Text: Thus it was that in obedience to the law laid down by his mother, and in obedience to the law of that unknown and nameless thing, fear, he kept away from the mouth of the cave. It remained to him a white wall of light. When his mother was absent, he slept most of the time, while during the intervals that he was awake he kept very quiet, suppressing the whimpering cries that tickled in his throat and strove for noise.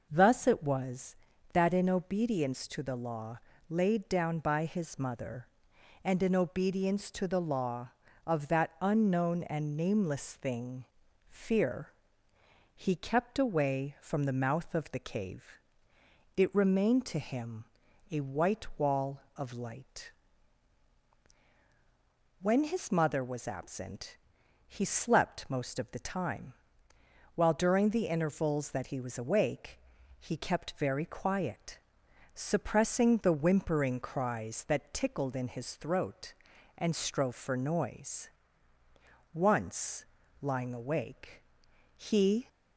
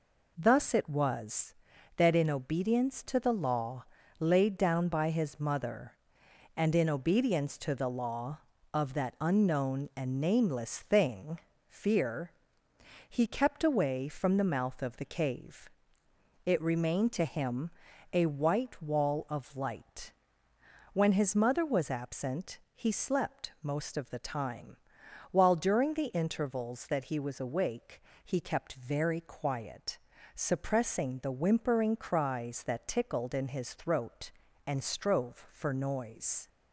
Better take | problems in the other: second | pauses between "law" and "laid"; slight; at 3.3 s; 0.30 s long; slight in the second // pauses between "him" and "a"; noticeable; at 17.6 s; 0.48 s long; also in the second // pauses between "awake" and "he"; at 29.7 s; 0.42 s long; slight in the second // goes on to say "Once lying awake he"; strong; from 39.3 s on; 3.1 s long

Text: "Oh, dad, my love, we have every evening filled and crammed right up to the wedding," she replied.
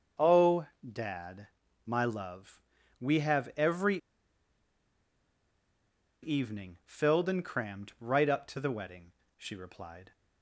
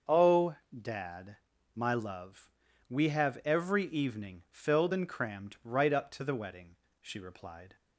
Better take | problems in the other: second | starts louder than the rest; until 1.3 s; 6.5 dB; also in the second // pauses between "every" and "evening"; strong; at 3.9 s; 2.2 s long

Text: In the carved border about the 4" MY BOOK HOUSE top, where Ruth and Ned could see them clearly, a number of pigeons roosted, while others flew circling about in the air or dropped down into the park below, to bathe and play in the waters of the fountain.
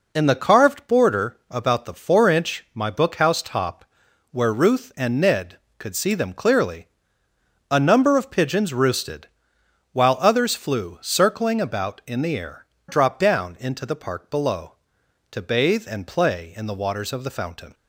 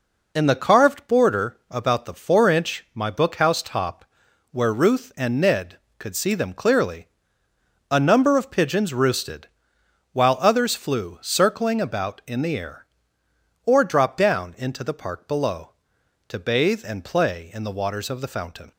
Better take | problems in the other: second | skips "or"; at 12.7 s

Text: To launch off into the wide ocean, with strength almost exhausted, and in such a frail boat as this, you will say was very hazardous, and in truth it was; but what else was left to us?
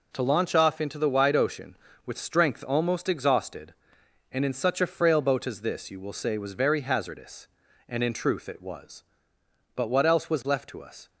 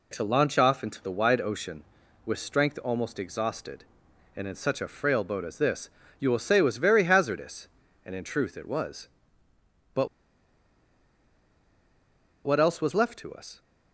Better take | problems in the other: first | pauses between "but" and "what"; strong; at 10.0 s; 2.3 s long

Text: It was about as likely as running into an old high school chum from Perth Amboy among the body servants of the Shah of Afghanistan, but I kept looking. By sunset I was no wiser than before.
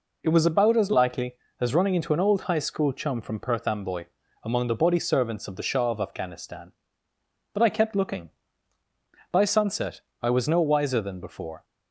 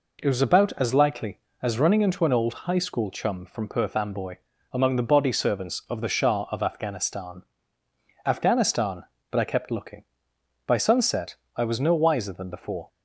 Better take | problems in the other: first | pauses between "Amboy" and "among"; slight; at 4.3 s; 0.34 s long; also in the first // says "Afghanistan" twice; at 8.2 s // pauses between "sunset" and "I"; slight; at 11.3 s; 0.20 s long; slight in the first

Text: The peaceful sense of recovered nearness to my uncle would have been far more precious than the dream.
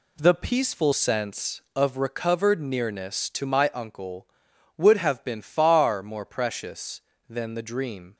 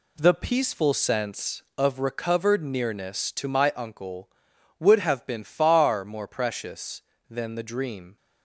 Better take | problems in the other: neither | none

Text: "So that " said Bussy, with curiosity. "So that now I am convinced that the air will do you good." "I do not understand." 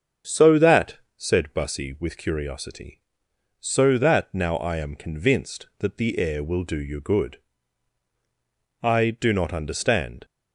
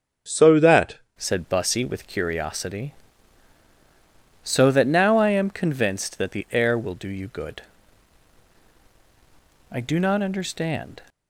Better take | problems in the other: first | starts louder than the rest; until 1.3 s; 6.5 dB; also in the first // changes voice at "said"; from 1.1 s on; 9.9 s long

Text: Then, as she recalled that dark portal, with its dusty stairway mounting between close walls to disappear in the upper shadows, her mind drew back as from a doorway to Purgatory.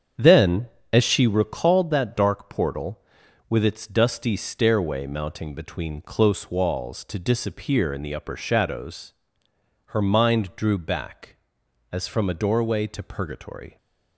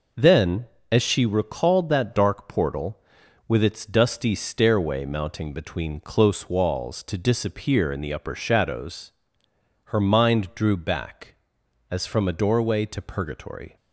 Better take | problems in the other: second | starts louder than the rest; strong; until 1.9 s; 7.5 dB

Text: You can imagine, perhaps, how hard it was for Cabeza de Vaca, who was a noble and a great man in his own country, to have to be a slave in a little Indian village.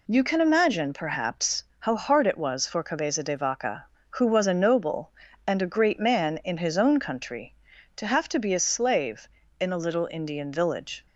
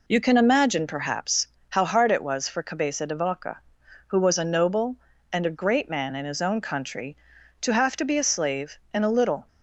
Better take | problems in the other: first | stops before "Indian village"; at 9.4 s

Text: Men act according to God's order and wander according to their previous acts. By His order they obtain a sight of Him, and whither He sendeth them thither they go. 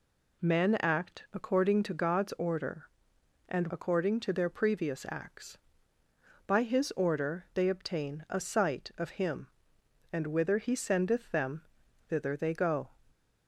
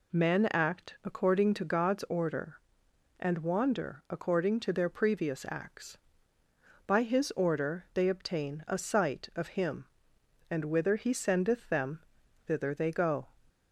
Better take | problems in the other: second | skips "wander"; at 3.6 s // pauses between "them" and "thither"; at 11.6 s; 0.44 s long; also in the second

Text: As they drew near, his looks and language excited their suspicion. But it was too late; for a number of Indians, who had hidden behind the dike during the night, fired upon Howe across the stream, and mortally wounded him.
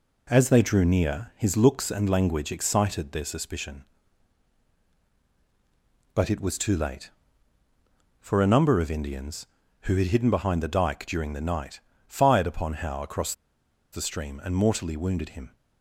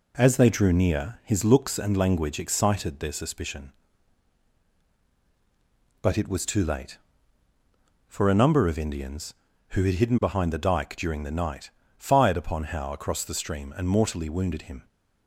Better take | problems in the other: second | pauses between "across" and "the"; noticeable; at 13.3 s; 0.60 s long

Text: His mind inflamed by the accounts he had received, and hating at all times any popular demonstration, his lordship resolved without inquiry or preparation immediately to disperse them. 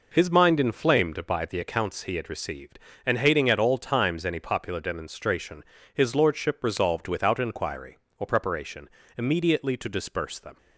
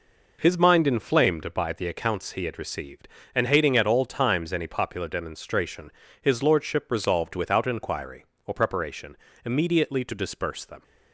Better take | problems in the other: neither | pauses between "preparation" and "immediately"; slight; the same in both

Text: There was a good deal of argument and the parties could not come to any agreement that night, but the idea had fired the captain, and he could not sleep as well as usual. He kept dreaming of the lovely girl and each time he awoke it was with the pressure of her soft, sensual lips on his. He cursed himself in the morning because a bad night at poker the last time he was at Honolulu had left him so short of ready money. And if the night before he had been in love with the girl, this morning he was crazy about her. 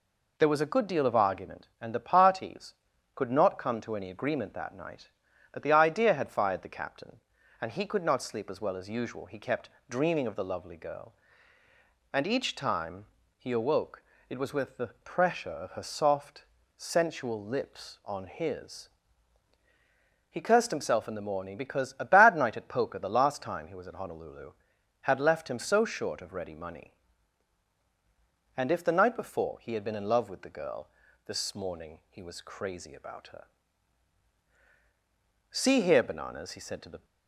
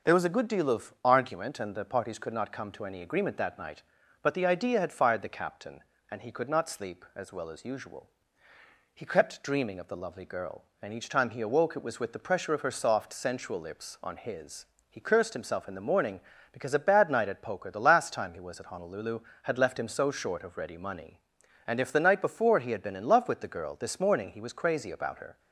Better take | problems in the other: second | pauses between "kept" and "dreaming"; slight; at 9.6 s; 0.20 s long // pauses between "time" and "he"; slight; at 13.0 s; 0.32 s long // pauses between "awoke" and "it"; slight; at 14.0 s; 0.26 s long // pauses between "the" and "pressure"; slight; at 14.8 s; 0.16 s long // goes on to say "See here Bananas he said to the"; from 35.5 s on; 1.5 s long

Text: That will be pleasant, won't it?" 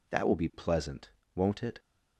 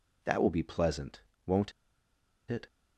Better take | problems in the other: first | pauses between "won't" and "it"; noticeable; at 1.7 s; 0.78 s long

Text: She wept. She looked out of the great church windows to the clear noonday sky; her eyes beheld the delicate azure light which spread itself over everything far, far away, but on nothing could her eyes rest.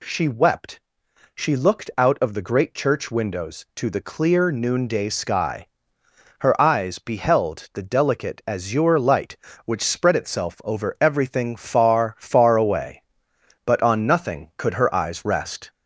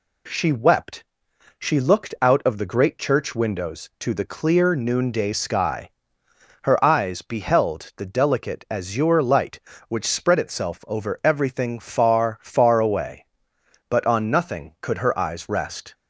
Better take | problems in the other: second | gets louder; slight; throughout; 2.5 dB

